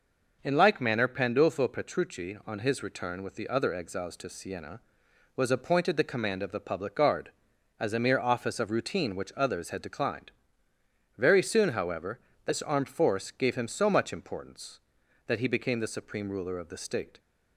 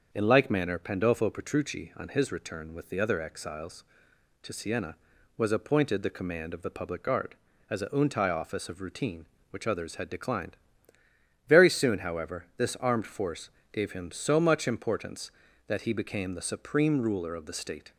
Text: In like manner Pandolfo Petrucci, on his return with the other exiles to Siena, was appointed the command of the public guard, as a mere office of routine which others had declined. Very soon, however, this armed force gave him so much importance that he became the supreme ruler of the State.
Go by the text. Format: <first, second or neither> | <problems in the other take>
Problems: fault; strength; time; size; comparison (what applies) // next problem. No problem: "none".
first | starts louder than the rest; until 1.1 s; 6.5 dB // says "untai" for "mere"; at 7.8 s // pauses between "force" and "gave"; slight; at 13.4 s; 0.22 s long